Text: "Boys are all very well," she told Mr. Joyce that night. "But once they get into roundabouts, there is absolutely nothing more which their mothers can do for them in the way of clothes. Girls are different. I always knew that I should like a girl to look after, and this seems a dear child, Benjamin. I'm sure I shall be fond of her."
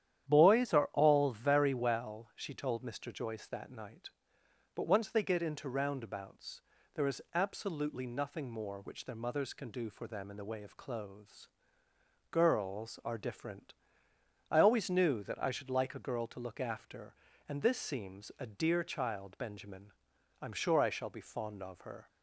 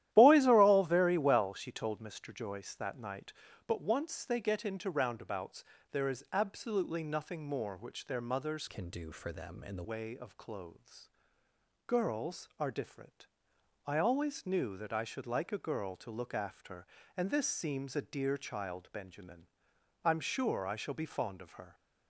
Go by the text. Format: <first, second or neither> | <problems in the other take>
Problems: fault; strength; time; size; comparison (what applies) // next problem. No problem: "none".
first | starts louder than the rest; strong; until 1.1 s; 12.5 dB; strong in the first // changes voice from "can" to "the"; from 8.6 to 9.8 s; 1.2 s long